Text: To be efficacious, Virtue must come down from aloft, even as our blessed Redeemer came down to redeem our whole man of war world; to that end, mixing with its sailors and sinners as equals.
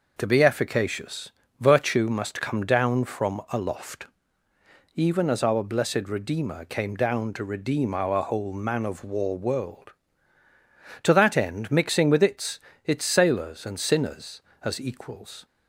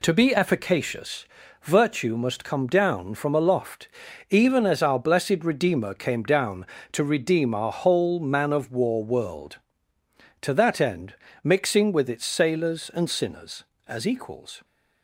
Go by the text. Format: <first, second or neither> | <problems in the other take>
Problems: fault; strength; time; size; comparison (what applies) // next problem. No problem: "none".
second | says "its" twice; at 12.8 s